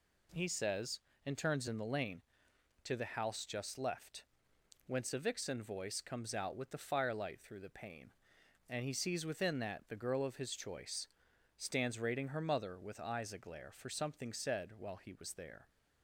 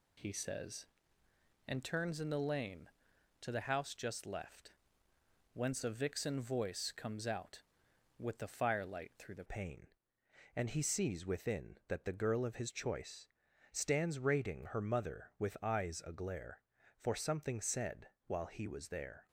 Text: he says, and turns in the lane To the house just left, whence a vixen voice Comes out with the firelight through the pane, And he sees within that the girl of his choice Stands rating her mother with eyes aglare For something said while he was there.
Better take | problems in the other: first | changes voice at "pane"; from 9.4 s on; 9.8 s long // pauses between "choice" and "Stands"; at 13.2 s; 0.44 s long; noticeable in the first // pauses between "said" and "while"; slight; at 18.0 s; 0.18 s long

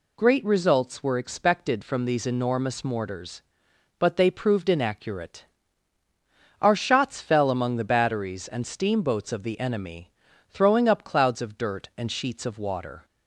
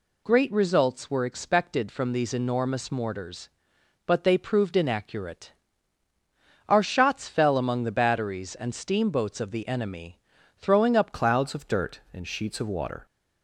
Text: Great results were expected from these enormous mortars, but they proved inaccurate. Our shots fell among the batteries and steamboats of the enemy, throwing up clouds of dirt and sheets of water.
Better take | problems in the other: first | changes voice at "clouds"; from 11.1 s on; 1.9 s long

